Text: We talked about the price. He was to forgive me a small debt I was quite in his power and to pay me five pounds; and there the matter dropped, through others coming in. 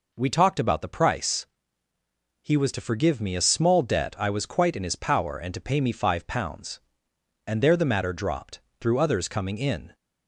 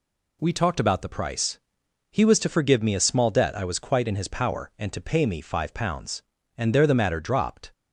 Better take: first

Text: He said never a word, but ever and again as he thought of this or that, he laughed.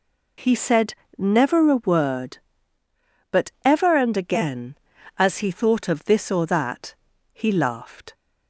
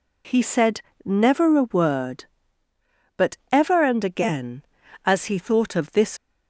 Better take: first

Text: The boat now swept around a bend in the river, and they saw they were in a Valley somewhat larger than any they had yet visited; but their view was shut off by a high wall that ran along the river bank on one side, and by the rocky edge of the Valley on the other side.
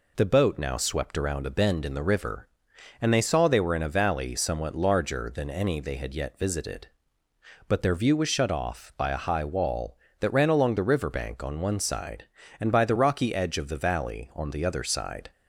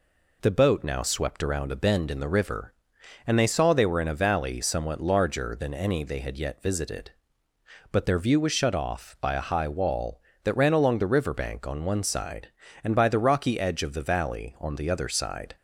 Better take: neither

